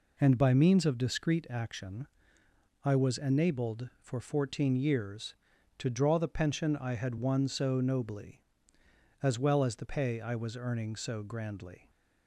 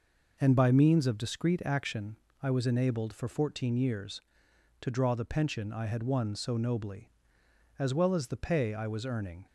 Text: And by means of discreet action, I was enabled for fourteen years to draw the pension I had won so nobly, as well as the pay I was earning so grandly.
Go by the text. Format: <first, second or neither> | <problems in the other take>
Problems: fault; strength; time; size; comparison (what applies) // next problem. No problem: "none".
first | stops before "so grandly"; at 9.4 s